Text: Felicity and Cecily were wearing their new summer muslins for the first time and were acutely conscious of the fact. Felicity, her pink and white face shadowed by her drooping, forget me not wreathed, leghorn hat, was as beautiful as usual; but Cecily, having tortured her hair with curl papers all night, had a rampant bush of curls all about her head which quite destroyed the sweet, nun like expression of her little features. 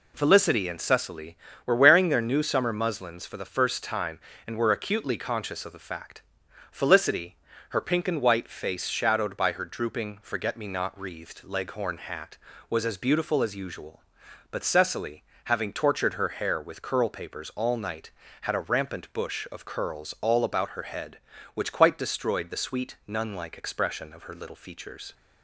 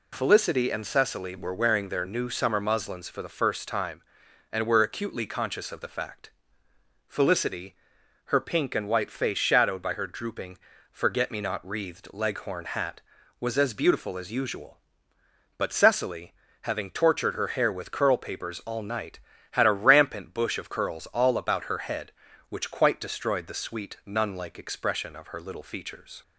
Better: neither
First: none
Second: none

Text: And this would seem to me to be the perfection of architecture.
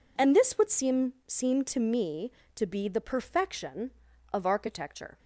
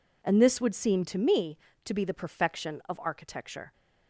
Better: second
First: says "seem" twice; at 1.2 s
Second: none

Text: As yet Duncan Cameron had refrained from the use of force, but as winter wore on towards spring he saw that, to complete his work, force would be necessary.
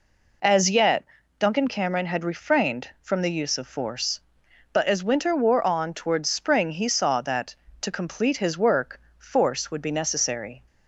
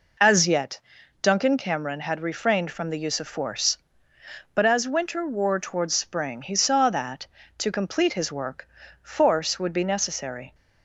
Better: first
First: pauses between "yet" and "Duncan"; slight; at 1.0 s; 0.36 s long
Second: pauses between "yet" and "Duncan"; at 0.8 s; 0.42 s long // skips "on"; at 5.6 s

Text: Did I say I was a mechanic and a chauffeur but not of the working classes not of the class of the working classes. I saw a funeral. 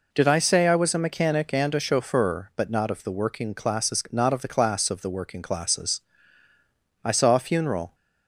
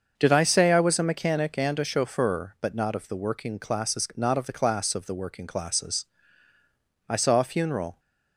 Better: first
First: none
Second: starts louder than the rest; until 1.3 s; 6.5 dB

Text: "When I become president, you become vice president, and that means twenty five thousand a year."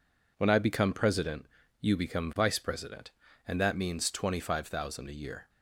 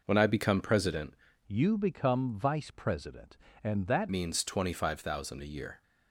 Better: first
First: none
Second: changes voice from "you" to "that"; from 1.4 to 4.0 s; 2.6 s long

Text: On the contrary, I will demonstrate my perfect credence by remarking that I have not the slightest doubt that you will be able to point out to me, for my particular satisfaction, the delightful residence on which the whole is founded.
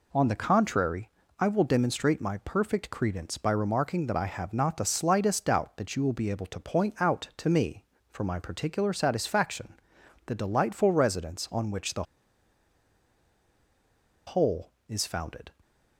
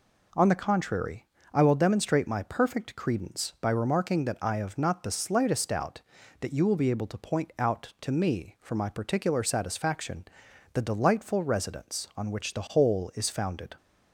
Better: second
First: pauses between "the" and "whole"; strong; at 12.0 s; 2.2 s long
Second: none

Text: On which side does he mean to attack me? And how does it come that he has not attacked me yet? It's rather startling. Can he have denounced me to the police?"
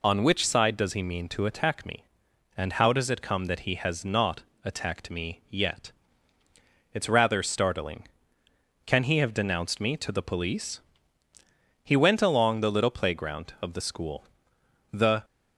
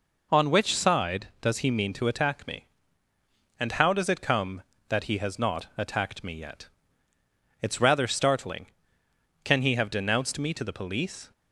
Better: second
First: pauses between "not" and "attacked"; slight; at 4.4 s; 0.20 s long // goes on to say "He went along the little playground of the school The"; strong; from 11.8 s on; 3.4 s long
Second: none

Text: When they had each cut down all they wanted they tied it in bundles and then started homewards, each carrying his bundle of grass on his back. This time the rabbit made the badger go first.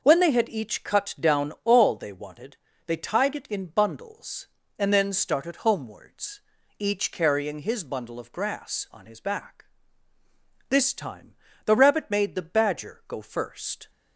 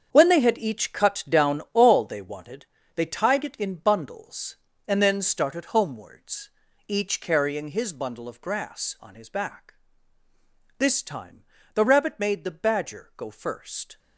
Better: first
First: pauses between "wanted" and "they"; slight; at 2.5 s; 0.30 s long // pauses between "time" and "the"; slight; at 11.3 s; 0.32 s long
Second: gets quieter; strong; throughout; 11 dB // pauses between "wanted" and "they"; slight; at 2.6 s; 0.30 s long // pauses between "time" and "the"; slight; at 11.4 s; 0.32 s long

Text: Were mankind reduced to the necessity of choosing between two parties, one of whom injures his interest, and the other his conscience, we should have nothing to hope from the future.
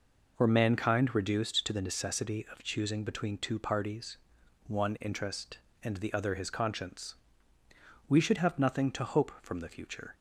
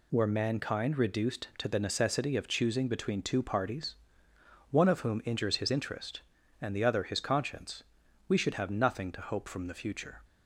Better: second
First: skips "of whom injures his"; at 4.9 s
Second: none

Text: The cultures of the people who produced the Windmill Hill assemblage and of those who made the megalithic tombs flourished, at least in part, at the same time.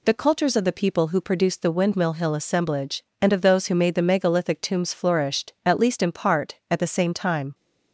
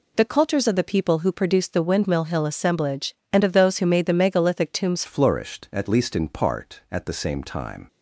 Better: first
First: none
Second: changes voice at "flourished"; from 5.0 s on; 2.8 s long

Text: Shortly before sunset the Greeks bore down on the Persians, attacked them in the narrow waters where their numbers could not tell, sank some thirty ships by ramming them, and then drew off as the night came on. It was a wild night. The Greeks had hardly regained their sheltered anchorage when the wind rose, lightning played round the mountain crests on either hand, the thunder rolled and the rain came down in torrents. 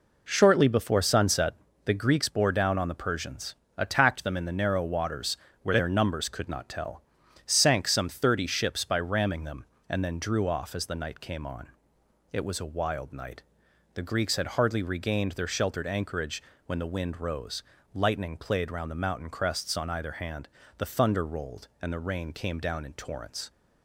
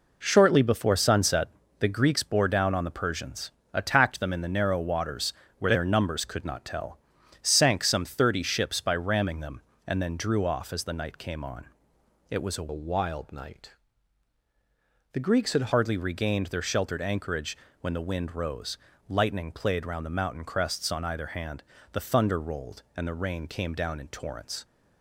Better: first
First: pauses between "sunset" and "the"; slight; at 1.5 s; 0.32 s long // pauses between "waters" and "where"; slight; at 5.3 s; 0.24 s long // pauses between "anchorage" and "when"; slight; at 16.4 s; 0.26 s long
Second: pauses between "sunset" and "the"; slight; at 1.4 s; 0.32 s long // pauses between "waters" and "where"; slight; at 5.3 s; 0.24 s long // changes voice from "wild" to "had"; from 12.7 to 15.7 s; 3.0 s long // pauses between "anchorage" and "when"; slight; at 17.5 s; 0.26 s long

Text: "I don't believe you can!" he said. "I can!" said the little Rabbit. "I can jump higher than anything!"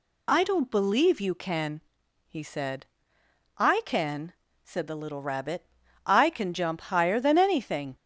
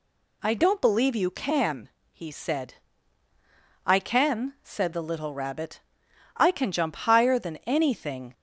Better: neither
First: none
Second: none

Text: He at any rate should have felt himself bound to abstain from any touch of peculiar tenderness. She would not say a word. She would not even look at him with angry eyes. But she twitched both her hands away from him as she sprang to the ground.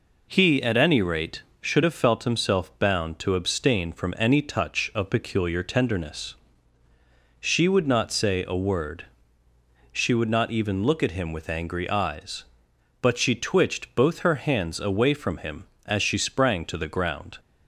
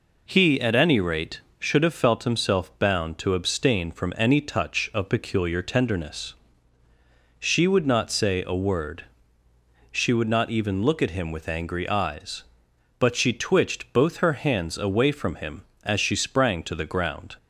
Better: neither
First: none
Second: none

